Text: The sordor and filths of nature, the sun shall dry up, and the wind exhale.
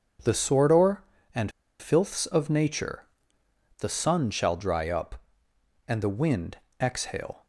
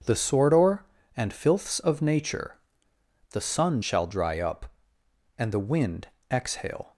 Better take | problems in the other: second | pauses between "and" and "filths"; slight; at 1.5 s; 0.29 s long // pauses between "wind" and "exhale"; slight; at 6.5 s; 0.24 s long; slight in the second

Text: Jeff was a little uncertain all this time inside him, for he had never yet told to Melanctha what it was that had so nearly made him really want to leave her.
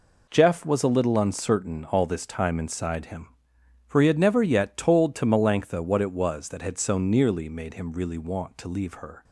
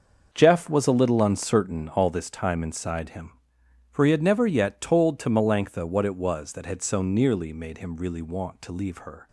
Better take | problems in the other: first | starts louder than the rest; until 2.3 s; 6.5 dB

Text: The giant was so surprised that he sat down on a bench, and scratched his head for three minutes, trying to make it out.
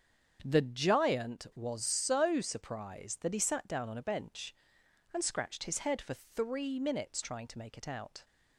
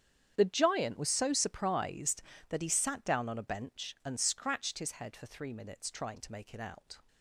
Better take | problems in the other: first | gets quieter; strong; throughout; 17.5 dB // starts louder than the rest; strong; until 1.3 s; 9 dB; strong in the first

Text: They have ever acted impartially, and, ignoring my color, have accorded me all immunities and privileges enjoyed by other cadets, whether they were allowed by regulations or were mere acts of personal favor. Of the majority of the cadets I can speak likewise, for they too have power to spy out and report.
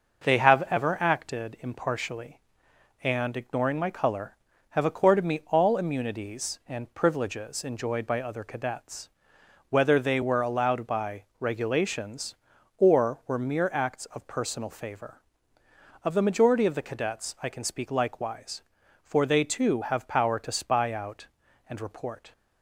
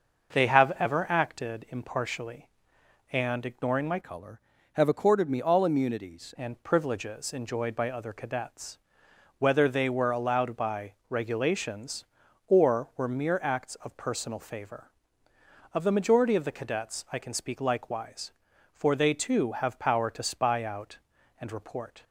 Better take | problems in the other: first | starts louder than the rest; noticeable; until 1.4 s; 6 dB // changes voice from "color" to "immunities"; from 4.0 to 6.3 s; 2.3 s long // pauses between "by" and "regulations"; slight; at 10.9 s; 0.16 s long; slight in the first

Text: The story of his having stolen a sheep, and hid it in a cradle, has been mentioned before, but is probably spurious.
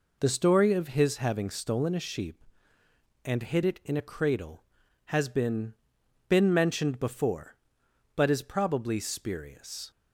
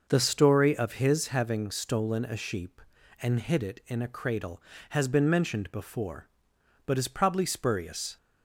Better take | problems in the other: second | says "been" twice; at 6.2 s

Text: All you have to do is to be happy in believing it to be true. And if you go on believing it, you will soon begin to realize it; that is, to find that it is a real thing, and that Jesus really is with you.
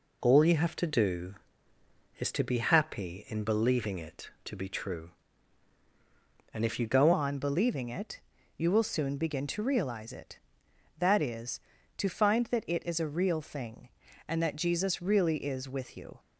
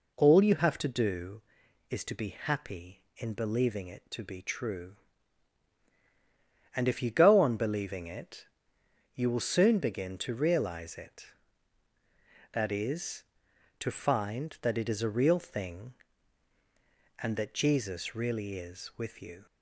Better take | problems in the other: second | changes voice at "on"; from 7.1 s on; 9.0 s long

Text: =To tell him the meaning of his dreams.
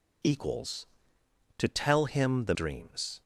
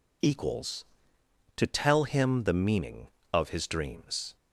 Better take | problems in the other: second | skips "meaning of his"; at 2.5 s

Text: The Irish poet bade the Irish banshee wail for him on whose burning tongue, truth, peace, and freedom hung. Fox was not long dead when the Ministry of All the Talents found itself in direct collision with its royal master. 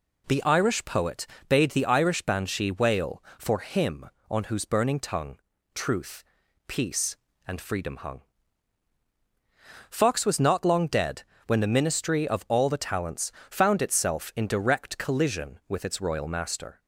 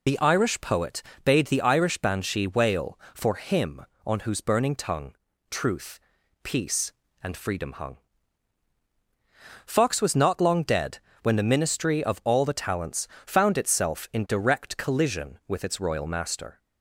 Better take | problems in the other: first | loses the start of "The"; at 0.0 s; 45 ms // pauses between "poet" and "bade"; slight; at 1.0 s; 0.24 s long; slight in the first // pauses between "dead" and "when"; slight; at 10.9 s; 0.22 s long; slight in the first // pauses between "Talents" and "found"; slight; at 13.0 s; 0.20 s long; slight in the first

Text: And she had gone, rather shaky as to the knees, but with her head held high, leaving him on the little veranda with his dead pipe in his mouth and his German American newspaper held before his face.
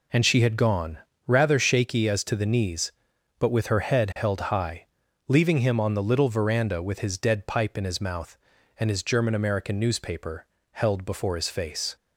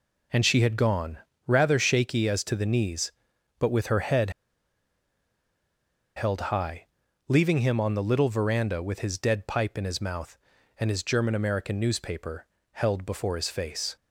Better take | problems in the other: first | pauses between "head" and "held"; strong; at 4.2 s; 1.8 s long // pauses between "newspaper" and "held"; slight; at 12.4 s; 0.28 s long; slight in the first

